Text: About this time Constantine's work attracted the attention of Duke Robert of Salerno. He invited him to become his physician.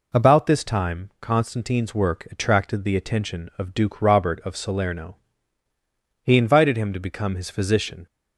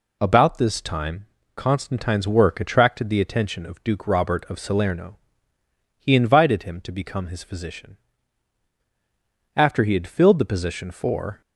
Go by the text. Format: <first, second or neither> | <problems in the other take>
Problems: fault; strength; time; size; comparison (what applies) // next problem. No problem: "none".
first | pauses between "time" and "Constantine's"; slight; at 1.2 s; 0.32 s long // goes on to say "After he had filled the position for"; strong; from 9.5 s on; 1.8 s long